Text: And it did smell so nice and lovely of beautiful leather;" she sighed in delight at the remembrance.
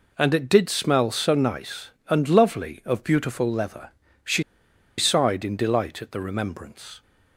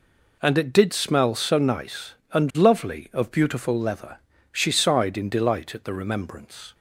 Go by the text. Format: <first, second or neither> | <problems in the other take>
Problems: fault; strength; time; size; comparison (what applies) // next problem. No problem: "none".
second | pauses between "she" and "sighed"; noticeable; at 4.4 s; 0.56 s long